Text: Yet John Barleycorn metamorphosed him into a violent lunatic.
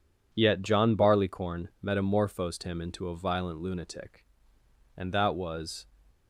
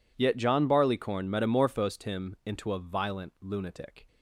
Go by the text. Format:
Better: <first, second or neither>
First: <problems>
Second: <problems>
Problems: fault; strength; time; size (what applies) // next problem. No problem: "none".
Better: second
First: goes on to say "And that was"; noticeable; from 4.9 s on; 0.90 s long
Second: none